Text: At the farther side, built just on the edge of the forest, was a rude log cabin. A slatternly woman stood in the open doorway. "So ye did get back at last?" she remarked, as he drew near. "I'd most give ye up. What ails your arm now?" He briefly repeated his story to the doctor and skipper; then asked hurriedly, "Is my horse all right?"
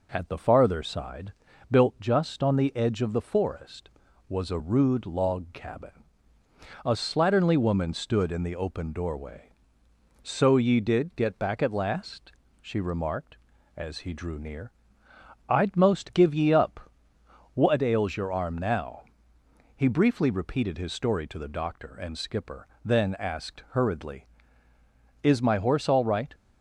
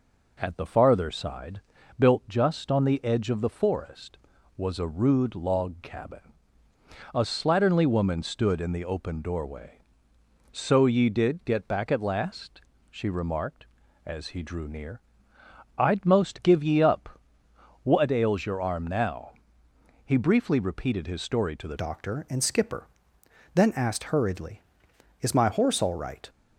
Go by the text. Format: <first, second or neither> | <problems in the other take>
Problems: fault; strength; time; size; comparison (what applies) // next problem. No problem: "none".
first | changes voice at "doctor"; from 21.7 s on; 4.5 s long